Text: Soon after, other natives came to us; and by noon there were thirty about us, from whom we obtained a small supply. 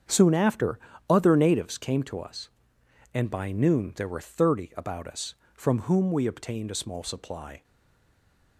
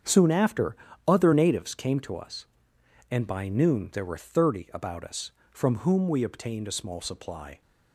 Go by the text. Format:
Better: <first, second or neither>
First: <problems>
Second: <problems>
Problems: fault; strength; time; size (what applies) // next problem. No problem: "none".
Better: second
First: starts louder than the rest; strong; until 1.3 s; 7.5 dB // stays silent after the last word; from 7.6 s on; 0.9 s long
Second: starts louder than the rest; strong; until 1.3 s; 7.5 dB